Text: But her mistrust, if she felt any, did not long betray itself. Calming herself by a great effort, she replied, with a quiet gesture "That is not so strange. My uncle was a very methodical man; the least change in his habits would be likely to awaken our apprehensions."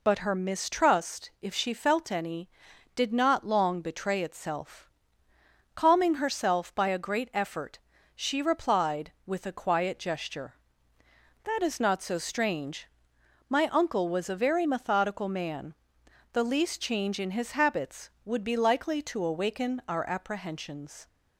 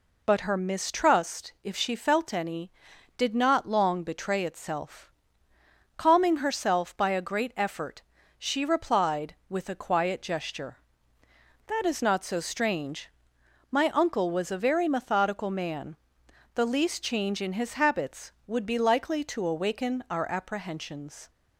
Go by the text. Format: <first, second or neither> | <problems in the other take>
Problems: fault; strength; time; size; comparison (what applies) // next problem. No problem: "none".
neither | none